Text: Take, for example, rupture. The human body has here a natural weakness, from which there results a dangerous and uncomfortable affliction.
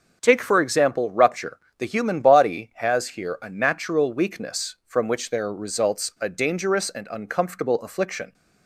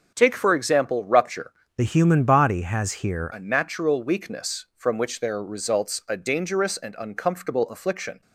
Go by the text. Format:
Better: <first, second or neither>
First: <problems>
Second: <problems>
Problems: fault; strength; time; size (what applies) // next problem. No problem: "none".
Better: first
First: starts louder than the rest; noticeable; until 1.2 s; 6 dB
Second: starts louder than the rest; noticeable; until 1.1 s; 6 dB // changes voice from "The" to "here"; from 1.7 to 3.3 s; 1.6 s long